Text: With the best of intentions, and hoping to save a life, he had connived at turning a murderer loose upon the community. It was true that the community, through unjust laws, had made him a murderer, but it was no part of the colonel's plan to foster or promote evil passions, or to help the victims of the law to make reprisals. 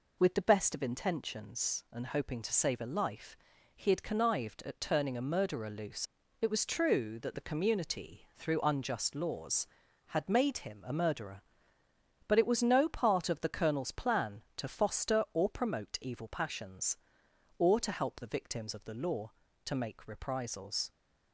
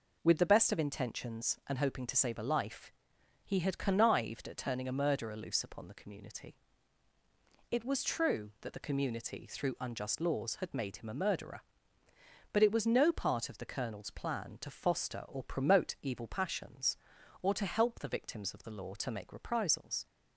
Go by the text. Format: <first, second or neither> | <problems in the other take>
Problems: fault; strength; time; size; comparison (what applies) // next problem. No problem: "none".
second | skips "upon the community"; at 6.2 s